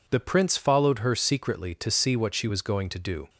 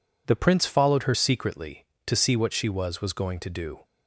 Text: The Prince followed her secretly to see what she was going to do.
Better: first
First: none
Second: says "was" twice; at 3.0 s

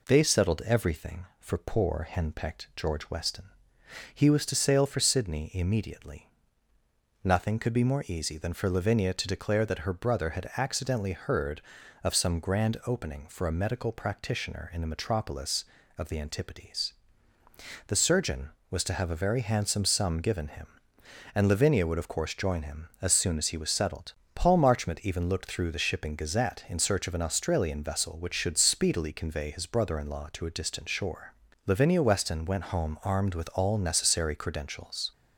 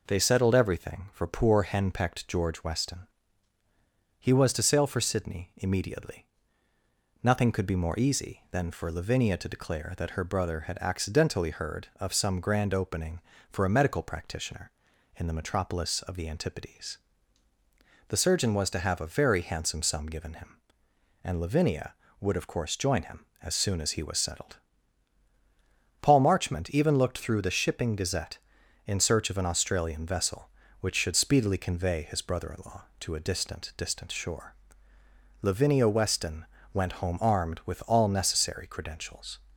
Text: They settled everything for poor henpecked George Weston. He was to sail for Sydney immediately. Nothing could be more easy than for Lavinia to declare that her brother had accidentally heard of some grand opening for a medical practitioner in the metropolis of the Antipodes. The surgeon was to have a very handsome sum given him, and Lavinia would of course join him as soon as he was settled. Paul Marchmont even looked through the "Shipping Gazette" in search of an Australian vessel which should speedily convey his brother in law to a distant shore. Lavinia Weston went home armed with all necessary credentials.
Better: first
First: none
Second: says "distant" twice; at 33.7 s // pauses between "Weston" and "went"; slight; at 36.4 s; 0.30 s long

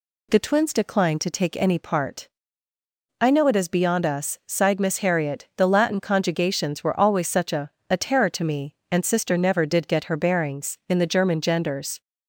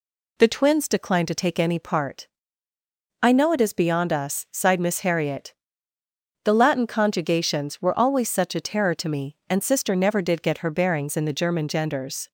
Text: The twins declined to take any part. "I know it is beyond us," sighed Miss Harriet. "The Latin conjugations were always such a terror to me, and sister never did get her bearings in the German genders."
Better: second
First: says "a" twice; at 7.8 s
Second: none

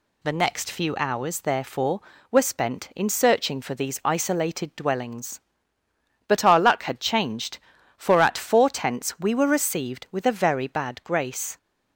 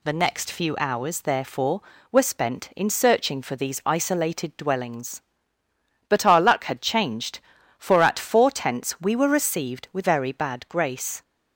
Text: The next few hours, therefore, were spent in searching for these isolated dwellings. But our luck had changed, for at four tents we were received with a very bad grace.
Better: first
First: none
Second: skips "a"; at 10.0 s

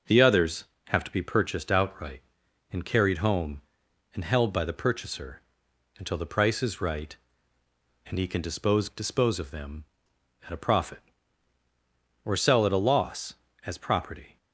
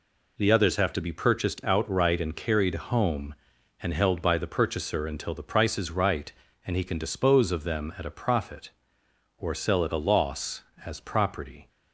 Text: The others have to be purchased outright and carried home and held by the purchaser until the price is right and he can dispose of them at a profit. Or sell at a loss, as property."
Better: second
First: pauses between "purchaser" and "until"; noticeable; at 5.4 s; 0.56 s long // says "dispose" twice; at 8.8 s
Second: none

